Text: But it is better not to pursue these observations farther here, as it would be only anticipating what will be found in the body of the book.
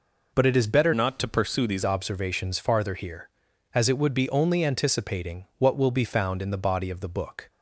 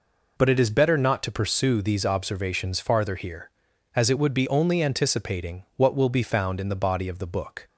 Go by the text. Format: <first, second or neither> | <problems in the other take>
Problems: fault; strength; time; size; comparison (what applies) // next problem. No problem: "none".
second | changes voice from "not" to "these"; from 0.9 to 1.8 s; 0.9 s long